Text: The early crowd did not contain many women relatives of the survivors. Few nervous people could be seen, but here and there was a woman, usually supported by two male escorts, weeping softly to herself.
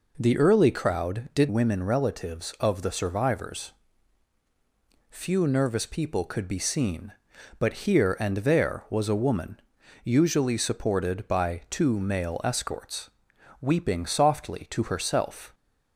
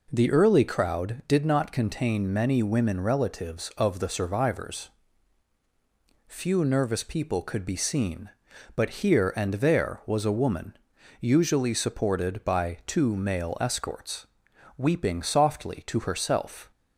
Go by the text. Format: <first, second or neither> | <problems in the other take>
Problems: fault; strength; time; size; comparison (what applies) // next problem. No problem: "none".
second | skips "not contain many"; at 1.4 s